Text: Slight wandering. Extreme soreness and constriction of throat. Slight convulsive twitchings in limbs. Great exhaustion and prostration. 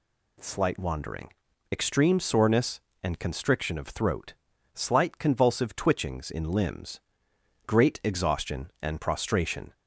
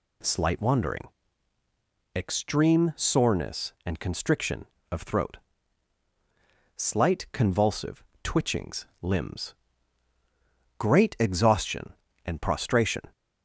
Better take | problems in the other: first | pauses between "convulsive" and "twitchings"; slight; at 8.0 s; 0.20 s long // skips "in"; at 8.9 s

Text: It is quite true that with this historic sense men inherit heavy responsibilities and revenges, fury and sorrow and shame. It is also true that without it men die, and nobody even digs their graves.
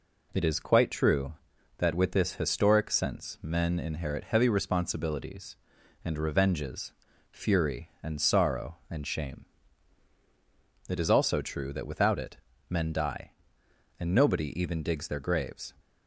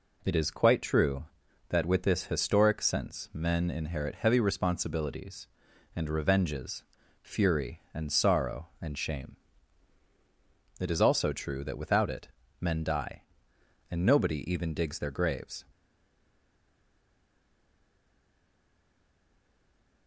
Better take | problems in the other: first | pauses between "it" and "men"; slight; at 12.2 s; 0.32 s long; slight in the first // stays silent after the last word; strong; from 15.7 s on; 4.3 s long

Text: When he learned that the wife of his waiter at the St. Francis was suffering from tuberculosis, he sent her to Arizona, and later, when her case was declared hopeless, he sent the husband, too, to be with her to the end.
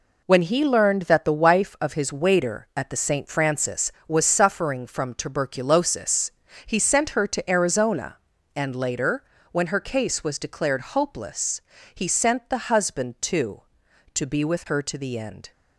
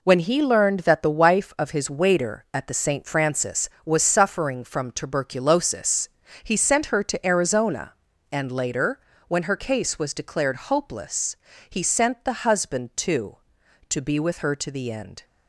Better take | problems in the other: neither | none

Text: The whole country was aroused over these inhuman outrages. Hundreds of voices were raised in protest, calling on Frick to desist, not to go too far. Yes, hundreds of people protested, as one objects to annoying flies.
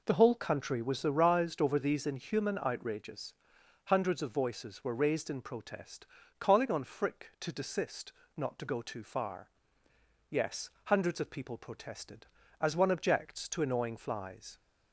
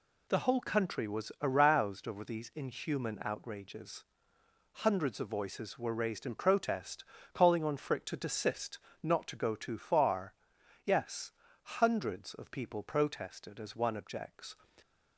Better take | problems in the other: first | stops before "to annoying flies"; at 14.8 s

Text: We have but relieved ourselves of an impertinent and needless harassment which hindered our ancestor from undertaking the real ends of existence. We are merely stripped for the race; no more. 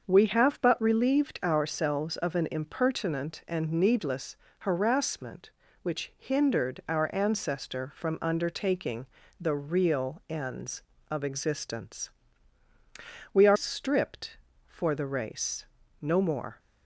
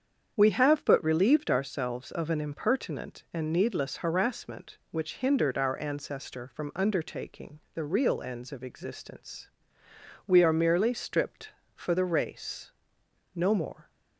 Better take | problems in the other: second | starts louder than the rest; until 1.0 s; 6.5 dB; strong in the second // pauses between "needless" and "harassment"; slight; at 4.3 s; 0.22 s long // pauses between "undertaking" and "the"; slight; at 9.0 s; 0.34 s long // skips "merely"; at 13.5 s

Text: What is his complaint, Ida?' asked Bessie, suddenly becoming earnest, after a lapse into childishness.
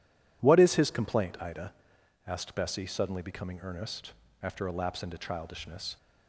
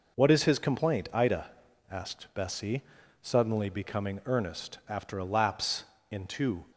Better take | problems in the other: first | pauses between "lapse" and "into"; slight; at 5.8 s; 0.26 s long // stops before "childishness"; at 6.7 s

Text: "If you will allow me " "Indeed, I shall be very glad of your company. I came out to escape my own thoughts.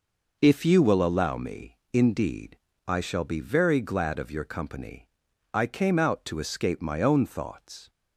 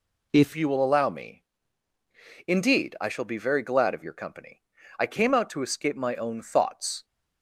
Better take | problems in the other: first | changes voice at "you"; from 0.5 s on; 6.5 s long

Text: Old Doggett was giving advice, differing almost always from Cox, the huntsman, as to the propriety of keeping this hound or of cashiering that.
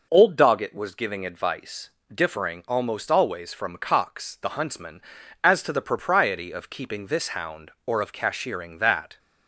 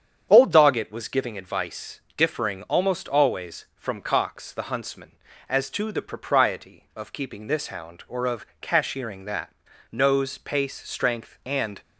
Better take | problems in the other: first | starts louder than the rest; strong; until 1.3 s; 8 dB // pauses between "of" and "cashiering"; slight; at 8.4 s; 0.16 s long // goes on to say "Nose pace strength and"; strong; from 9.9 s on; 1.9 s long

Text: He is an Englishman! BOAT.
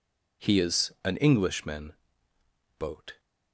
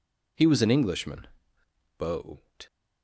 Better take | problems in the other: first | says "was" for "is"; at 0.4 s

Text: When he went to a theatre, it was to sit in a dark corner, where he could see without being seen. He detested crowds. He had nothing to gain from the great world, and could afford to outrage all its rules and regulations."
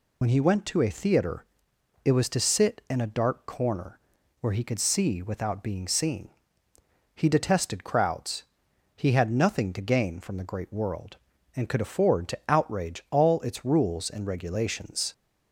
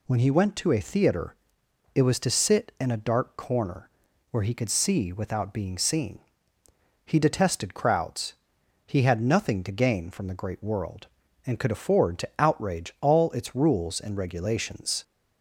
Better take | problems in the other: second | loses the start of "When"; at 0.2 s; 50 ms

